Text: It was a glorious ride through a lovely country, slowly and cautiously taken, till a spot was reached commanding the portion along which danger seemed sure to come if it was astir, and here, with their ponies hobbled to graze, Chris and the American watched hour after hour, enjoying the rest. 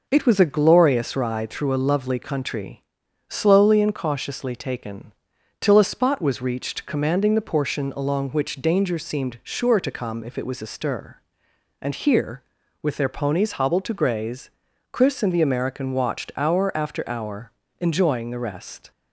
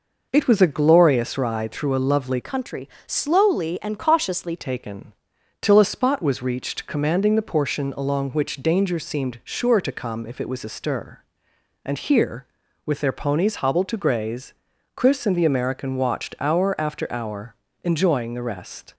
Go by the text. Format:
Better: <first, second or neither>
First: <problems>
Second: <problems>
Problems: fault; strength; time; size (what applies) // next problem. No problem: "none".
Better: first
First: none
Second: changes voice from "country" to "cautiously"; from 2.4 to 4.5 s; 2.1 s long